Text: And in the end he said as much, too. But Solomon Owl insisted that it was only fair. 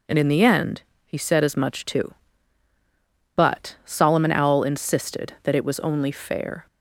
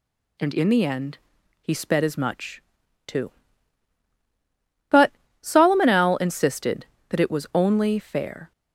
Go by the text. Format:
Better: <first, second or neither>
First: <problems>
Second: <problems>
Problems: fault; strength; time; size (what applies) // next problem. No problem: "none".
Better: first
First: pauses between "end" and "he"; slight; at 0.8 s; 0.24 s long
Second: pauses between "end" and "he"; at 1.1 s; 0.44 s long // says "sped" for "said"; at 1.7 s // pauses between "But" and "Solomon"; slight; at 5.1 s; 0.30 s long